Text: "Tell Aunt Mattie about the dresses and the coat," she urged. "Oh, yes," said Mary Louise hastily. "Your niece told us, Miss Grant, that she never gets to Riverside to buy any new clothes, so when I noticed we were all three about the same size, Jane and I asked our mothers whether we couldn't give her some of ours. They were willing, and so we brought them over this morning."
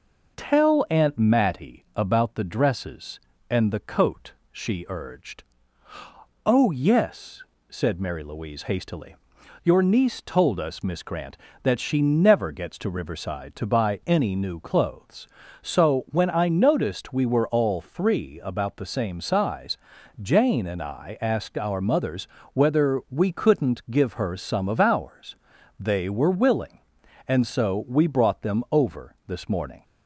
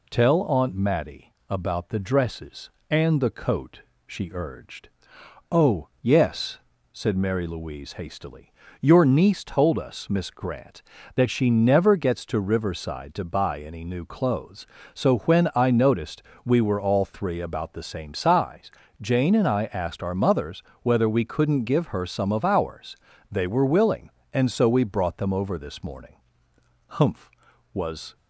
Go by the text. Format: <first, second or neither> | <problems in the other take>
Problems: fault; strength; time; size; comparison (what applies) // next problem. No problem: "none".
first | pauses between "Mattie" and "about"; slight; at 1.3 s; 0.16 s long // pauses between "noticed" and "we"; slight; at 16.2 s; 0.22 s long // pauses between "mothers" and "whether"; slight; at 20.6 s; 0.20 s long; slight in the first // goes on to say "Humph was"; noticeable; from 26.9 s on; 1.2 s long